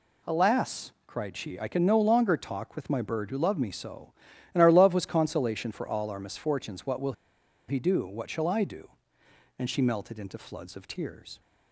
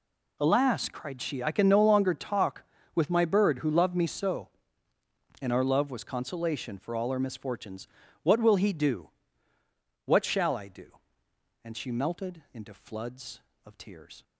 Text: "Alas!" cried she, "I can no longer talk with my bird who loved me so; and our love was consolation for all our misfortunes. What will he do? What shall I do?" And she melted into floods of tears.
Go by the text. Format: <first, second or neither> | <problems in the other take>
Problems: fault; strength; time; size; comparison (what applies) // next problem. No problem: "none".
second | pauses between "will" and "he"; noticeable; at 7.1 s; 0.55 s long